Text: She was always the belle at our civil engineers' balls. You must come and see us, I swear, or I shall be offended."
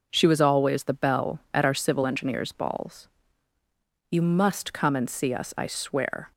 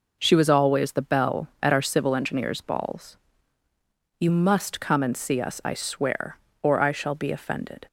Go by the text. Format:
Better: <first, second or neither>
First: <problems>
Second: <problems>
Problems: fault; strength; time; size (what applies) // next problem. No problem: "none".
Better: second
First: stops before "or I shall be offended"; at 6.3 s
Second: none